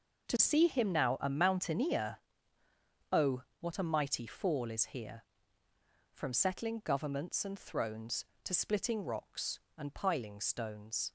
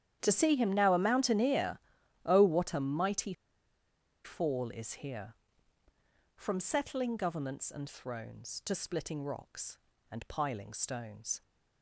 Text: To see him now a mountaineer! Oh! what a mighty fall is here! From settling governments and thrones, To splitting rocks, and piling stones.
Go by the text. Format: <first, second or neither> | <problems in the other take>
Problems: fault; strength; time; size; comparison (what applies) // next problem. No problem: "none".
first | starts louder than the rest; strong; until 1.2 s; 10 dB // pauses between "mighty" and "fall"; noticeable; at 3.3 s; 0.92 s long